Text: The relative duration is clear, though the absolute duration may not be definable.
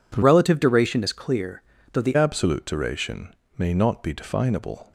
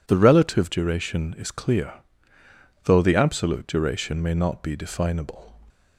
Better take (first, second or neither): second